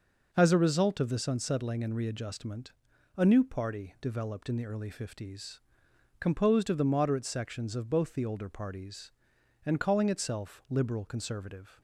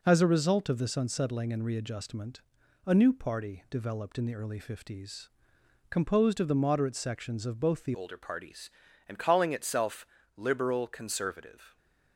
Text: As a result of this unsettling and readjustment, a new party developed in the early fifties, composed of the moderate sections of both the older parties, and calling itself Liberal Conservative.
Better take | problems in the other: first | changes voice at "older"; from 7.9 s on; 3.8 s long // pauses between "itself" and "Liberal"; slight; at 10.0 s; 0.28 s long

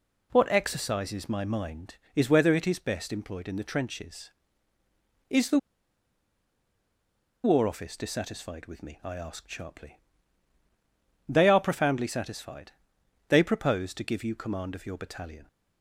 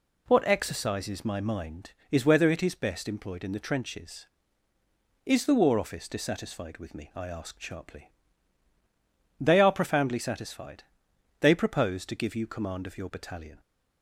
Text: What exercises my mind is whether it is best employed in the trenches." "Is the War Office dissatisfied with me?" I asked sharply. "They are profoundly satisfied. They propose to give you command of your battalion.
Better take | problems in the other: second | pauses between "the" and "War"; strong; at 5.5 s; 1.8 s long

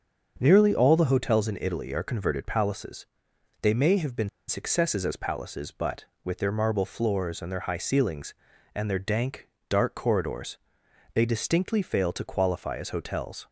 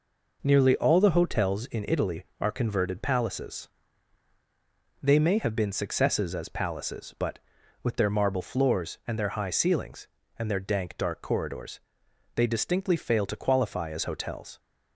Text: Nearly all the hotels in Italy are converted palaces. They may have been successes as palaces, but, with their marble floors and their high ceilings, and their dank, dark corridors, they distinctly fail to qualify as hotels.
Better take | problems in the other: second | starts louder than the rest; until 1.3 s; 7 dB // pauses between "been" and "successes"; slight; at 4.2 s; 0.19 s long

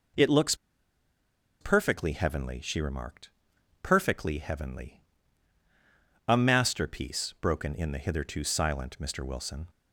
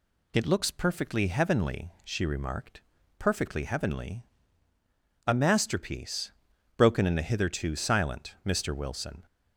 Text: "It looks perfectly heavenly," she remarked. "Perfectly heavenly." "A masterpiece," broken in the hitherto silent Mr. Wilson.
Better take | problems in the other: second | pauses between "looks" and "perfectly"; at 0.5 s; 1.0 s long

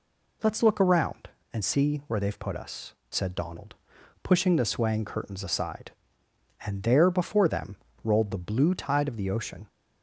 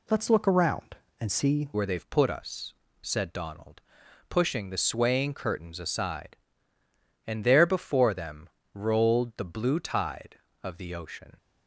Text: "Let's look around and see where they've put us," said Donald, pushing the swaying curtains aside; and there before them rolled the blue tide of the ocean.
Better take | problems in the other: first | changes voice at "where"; from 1.7 s on; 9.6 s long // pauses between "them" and "rolled"; slight; at 8.4 s; 0.24 s long; slight in the first

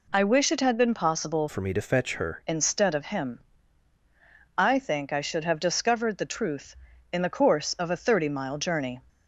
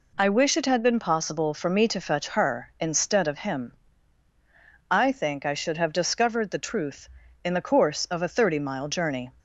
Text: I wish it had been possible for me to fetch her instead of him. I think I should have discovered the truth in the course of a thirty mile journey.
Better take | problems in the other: second | changes voice from "for" to "her"; from 1.4 to 2.4 s; 1.0 s long

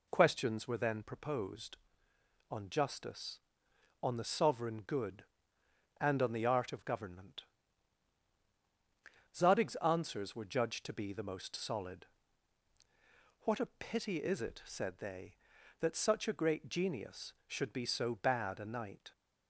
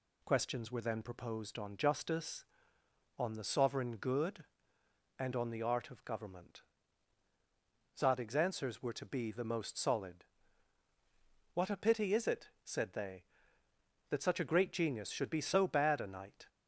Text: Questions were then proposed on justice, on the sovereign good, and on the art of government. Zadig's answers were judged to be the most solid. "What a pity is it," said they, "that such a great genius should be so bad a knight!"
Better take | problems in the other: first | skips "judged"; at 8.9 s

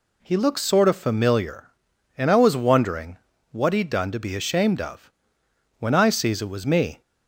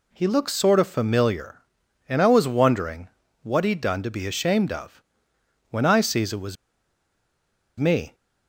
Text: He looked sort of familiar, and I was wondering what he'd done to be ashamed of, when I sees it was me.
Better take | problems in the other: first | pauses between "wondering" and "what"; slight; at 3.0 s; 0.34 s long; slight in the first // pauses between "was" and "me"; strong; at 6.5 s; 1.2 s long

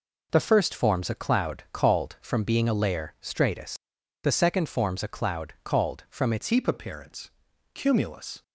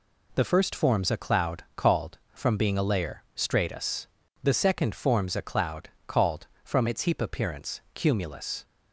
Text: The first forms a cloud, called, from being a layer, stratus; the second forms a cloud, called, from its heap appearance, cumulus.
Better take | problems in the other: second | changes voice at "heap"; from 6.5 s on; 1.9 s long

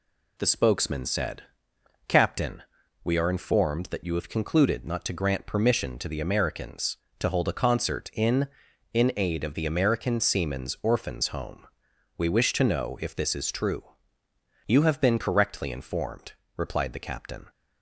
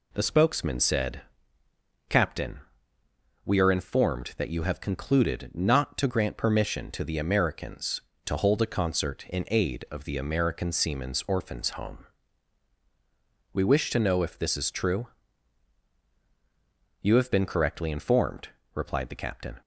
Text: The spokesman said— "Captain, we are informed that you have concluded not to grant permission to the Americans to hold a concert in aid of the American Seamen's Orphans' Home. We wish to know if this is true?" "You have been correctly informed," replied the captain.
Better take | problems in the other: second | says "in" twice; at 8.9 s

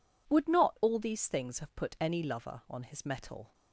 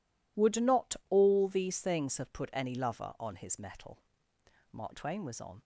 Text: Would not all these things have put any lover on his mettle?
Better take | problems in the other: first | goes on to say "Mark Twain was on"; noticeable; from 4.7 s on; 0.88 s long

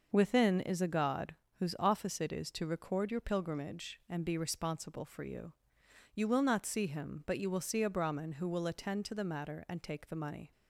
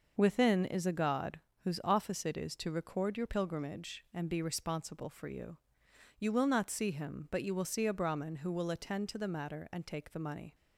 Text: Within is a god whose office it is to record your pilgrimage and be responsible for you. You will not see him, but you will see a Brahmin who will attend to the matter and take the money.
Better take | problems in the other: neither | pauses between "god" and "whose"; slight; the same in both

